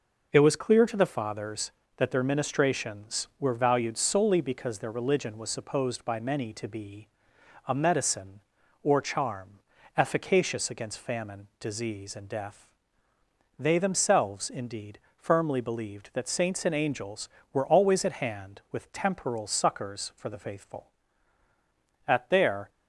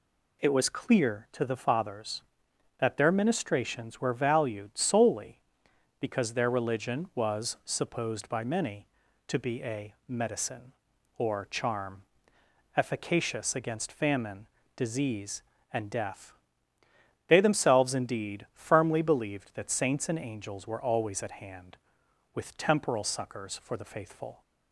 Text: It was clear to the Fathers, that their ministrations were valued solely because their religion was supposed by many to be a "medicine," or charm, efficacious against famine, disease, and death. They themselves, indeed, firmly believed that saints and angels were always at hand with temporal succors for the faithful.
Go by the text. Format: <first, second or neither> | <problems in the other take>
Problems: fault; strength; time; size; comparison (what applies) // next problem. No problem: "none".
second | pauses between "be" and "a"; noticeable; at 7.0 s; 0.58 s long // goes on to say "At their"; noticeable; from 22.0 s on; 0.62 s long